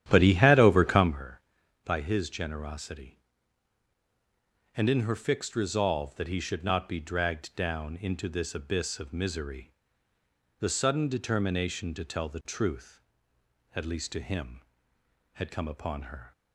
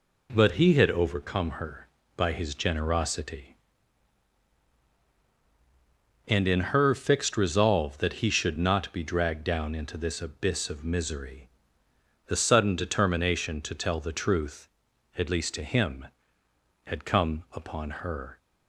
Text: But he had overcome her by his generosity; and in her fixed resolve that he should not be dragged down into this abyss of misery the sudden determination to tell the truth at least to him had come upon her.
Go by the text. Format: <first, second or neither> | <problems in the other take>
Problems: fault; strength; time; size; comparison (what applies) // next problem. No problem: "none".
second | starts louder than the rest; strong; until 1.2 s; 11 dB // pauses between "misery" and "the"; noticeable; at 9.7 s; 0.88 s long; noticeable in the second